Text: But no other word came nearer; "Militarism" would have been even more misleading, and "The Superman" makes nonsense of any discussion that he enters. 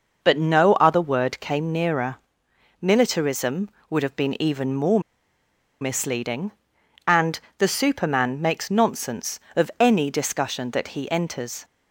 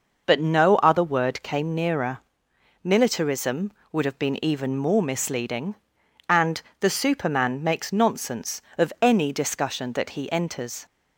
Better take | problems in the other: second | pauses between "more" and "misleading"; noticeable; at 4.9 s; 0.81 s long // pauses between "and" and "The"; slight; at 7.4 s; 0.16 s long; slight in the second

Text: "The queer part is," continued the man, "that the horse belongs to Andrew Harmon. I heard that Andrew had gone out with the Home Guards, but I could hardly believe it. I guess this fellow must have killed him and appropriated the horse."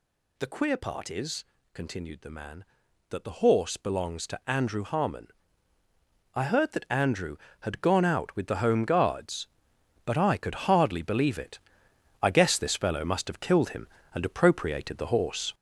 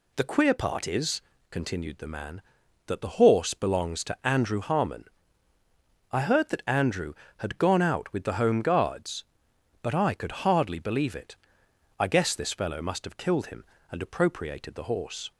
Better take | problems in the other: second | gets louder; throughout; 6.5 dB

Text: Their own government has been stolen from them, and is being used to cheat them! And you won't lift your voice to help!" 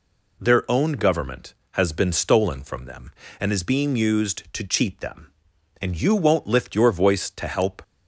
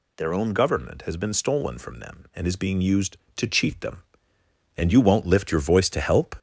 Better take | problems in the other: first | gets louder; slight; throughout; 3 dB

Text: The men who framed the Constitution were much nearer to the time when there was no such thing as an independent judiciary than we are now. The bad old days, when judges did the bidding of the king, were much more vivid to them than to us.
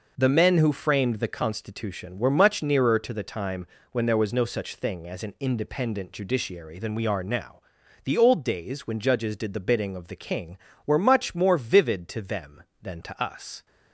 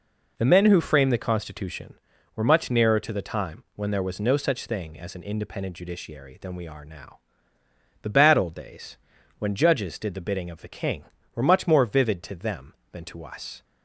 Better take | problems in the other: second | pauses between "time" and "when"; slight; at 3.6 s; 0.24 s long // skips "bad"; at 8.1 s

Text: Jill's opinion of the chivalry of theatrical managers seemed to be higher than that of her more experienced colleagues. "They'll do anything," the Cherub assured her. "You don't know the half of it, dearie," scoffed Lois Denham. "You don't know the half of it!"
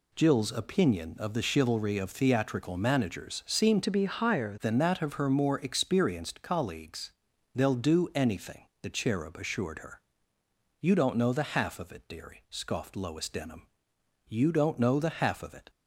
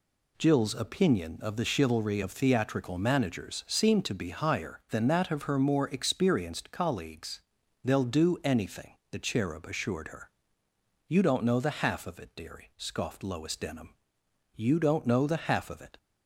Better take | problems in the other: second | changes voice from "to" to "higher"; from 3.8 to 4.5 s; 0.7 s long

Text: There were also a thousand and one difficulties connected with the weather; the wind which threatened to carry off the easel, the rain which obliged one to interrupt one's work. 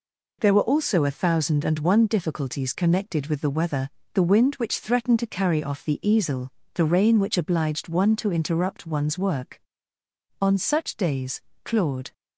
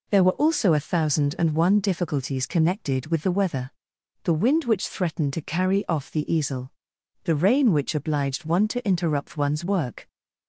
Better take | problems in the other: second | goes on to say "On such days Claude"; strong; from 10.4 s on; 1.7 s long

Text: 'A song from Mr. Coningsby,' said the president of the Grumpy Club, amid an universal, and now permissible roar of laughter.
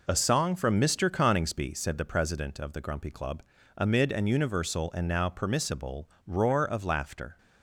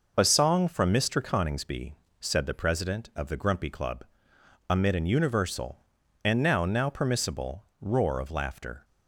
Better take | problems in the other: first | says "now" twice; at 6.6 s // pauses between "permissible" and "roar"; slight; at 7.6 s; 0.16 s long; slight in the first

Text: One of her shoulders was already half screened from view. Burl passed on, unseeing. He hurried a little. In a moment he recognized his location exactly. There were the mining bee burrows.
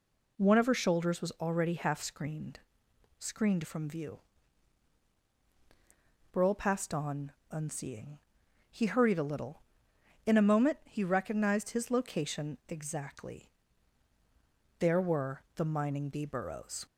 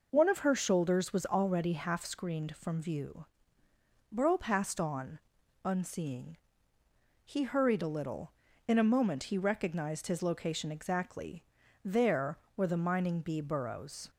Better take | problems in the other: second | says "screened" twice; at 3.1 s

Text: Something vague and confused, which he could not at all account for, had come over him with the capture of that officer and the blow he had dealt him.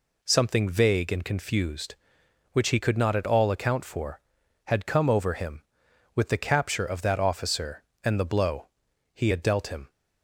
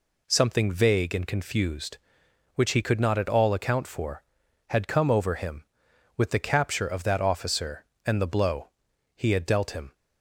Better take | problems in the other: neither | pauses between "blow" and "he"; noticeable; the same in both

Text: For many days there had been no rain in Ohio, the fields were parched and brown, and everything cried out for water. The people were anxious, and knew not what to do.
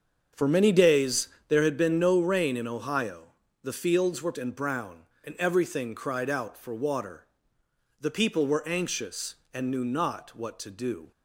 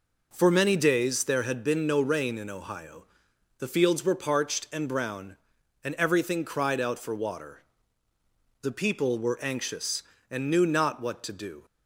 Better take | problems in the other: second | starts louder than the rest; until 1.5 s; 7 dB // pauses between "days" and "there"; slight; at 1.2 s; 0.20 s long // skips "parched"; at 4.3 s

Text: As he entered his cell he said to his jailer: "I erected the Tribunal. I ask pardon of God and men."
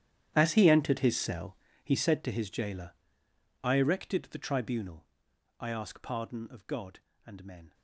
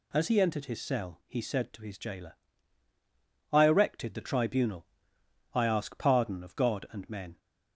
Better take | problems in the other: second | gets quieter; strong; throughout; 19 dB // pauses between "cell" and "he"; slight; at 1.5 s; 0.28 s long

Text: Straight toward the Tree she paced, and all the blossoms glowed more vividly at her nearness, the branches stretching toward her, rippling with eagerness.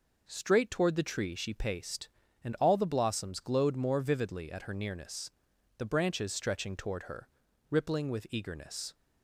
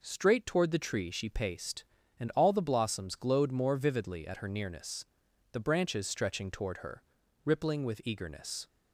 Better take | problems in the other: neither | none

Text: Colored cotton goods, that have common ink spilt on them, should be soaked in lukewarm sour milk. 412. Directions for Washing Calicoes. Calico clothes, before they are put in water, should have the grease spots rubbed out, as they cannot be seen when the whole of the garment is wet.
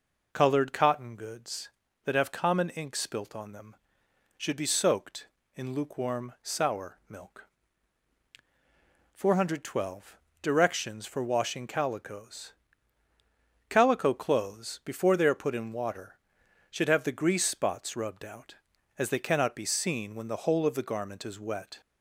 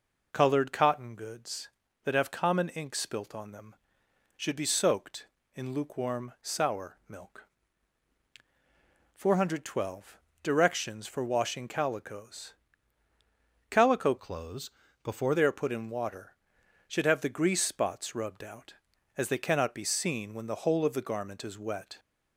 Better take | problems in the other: first | changes voice from "clothes" to "before"; from 14.1 to 15.3 s; 1.2 s long

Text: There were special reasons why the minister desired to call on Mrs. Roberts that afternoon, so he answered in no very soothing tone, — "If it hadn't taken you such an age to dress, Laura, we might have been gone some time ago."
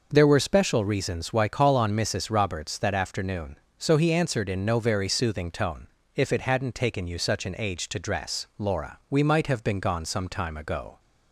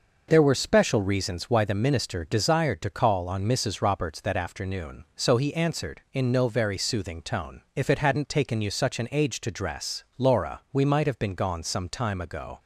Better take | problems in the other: second | skips "the minister desired to"; at 1.4 s

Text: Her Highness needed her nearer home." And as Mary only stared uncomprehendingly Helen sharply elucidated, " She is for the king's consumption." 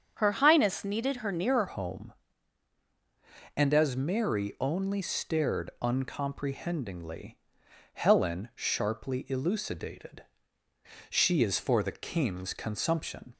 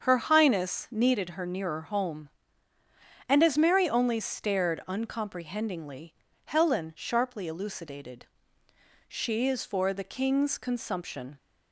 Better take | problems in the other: second | starts louder than the rest; strong; until 1.1 s; 7.5 dB; strong in the second // changes voice at "home"; from 1.6 s on; 11.7 s long // pauses between "uncomprehendingly" and "Helen"; noticeable; at 7.3 s; 0.56 s long; slight in the second

